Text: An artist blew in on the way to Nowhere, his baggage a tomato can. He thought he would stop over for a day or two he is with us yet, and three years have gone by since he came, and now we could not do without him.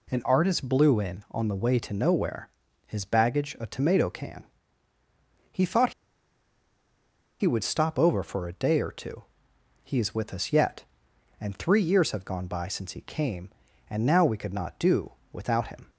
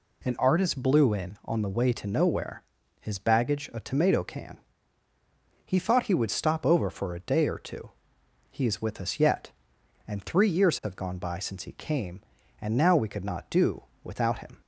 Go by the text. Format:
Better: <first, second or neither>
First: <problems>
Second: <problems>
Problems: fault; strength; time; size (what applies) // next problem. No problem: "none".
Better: second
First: pauses between "thought" and "he"; strong; at 5.9 s; 1.4 s long // pauses between "two" and "he"; noticeable; at 9.2 s; 0.64 s long // pauses between "do" and "without"; slight; at 15.1 s; 0.20 s long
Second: pauses between "two" and "he"; noticeable; at 7.9 s; 0.64 s long // pauses between "do" and "without"; slight; at 13.8 s; 0.20 s long